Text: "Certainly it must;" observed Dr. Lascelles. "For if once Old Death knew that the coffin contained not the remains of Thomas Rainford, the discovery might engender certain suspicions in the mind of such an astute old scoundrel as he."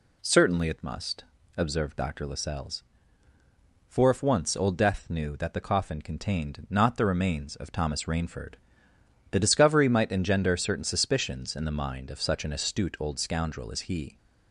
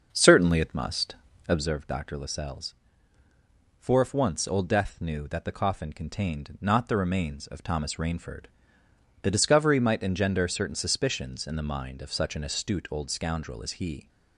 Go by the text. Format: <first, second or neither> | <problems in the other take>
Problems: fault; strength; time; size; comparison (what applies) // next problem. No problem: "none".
first | starts louder than the rest; until 1.7 s; 6.5 dB